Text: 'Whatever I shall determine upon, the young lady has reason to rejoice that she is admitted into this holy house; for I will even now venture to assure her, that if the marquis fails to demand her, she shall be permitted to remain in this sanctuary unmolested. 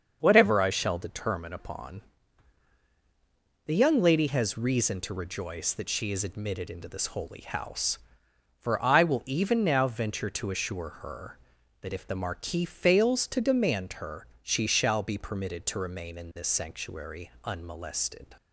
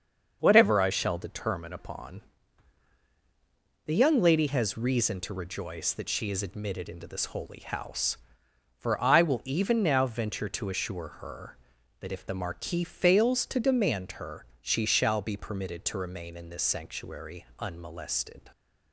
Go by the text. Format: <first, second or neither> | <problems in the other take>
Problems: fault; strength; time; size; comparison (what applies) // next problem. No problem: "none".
neither | starts louder than the rest; the same in both